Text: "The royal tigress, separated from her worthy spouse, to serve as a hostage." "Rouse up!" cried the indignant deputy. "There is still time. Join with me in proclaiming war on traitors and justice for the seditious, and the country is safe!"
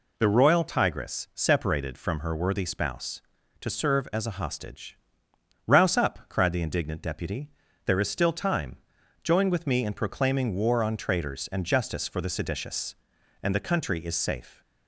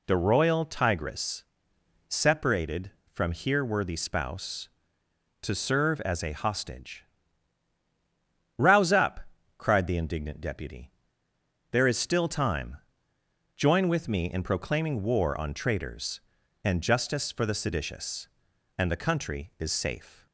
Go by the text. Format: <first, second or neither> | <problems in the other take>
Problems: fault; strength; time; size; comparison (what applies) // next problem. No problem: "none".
first | says "here" for "her"; at 3.3 s